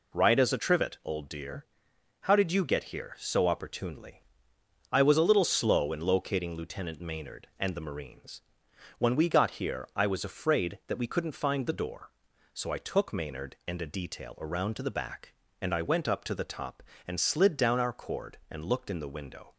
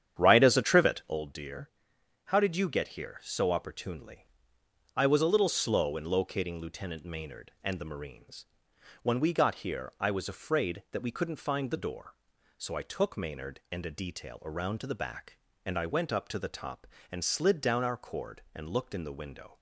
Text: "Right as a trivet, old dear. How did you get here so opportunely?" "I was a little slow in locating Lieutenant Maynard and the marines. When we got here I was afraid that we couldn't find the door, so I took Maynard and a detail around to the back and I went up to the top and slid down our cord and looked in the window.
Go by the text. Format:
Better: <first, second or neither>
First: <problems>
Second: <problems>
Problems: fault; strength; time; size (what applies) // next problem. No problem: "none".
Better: first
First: none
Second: starts louder than the rest; strong; until 1.2 s; 9 dB